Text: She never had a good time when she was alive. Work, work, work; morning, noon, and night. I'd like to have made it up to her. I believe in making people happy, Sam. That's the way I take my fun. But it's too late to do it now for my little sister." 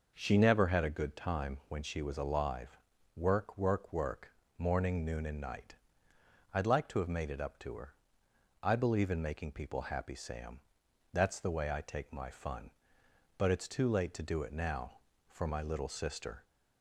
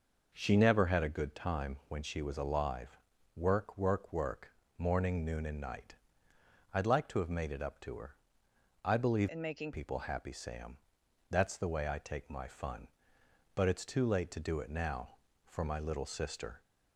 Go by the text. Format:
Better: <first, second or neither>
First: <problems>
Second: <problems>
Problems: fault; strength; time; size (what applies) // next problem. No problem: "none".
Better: first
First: none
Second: changes voice from "in" to "making"; from 9.2 to 9.7 s; 0.5 s long